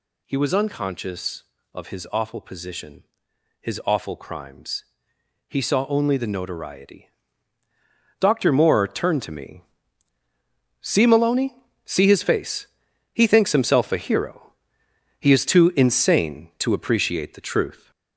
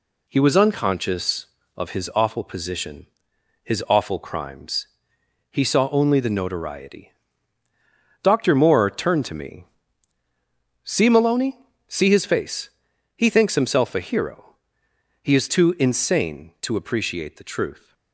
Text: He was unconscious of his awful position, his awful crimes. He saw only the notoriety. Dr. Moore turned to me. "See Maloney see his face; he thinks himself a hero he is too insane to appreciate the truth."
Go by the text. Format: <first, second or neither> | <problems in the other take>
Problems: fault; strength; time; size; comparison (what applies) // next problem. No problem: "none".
second | gets louder; noticeable; throughout; 4.5 dB // pauses between "Maloney" and "see"; slight; at 11.5 s; 0.30 s long; slight in the second // pauses between "hero" and "he"; noticeable; at 14.5 s; 0.68 s long; noticeable in the second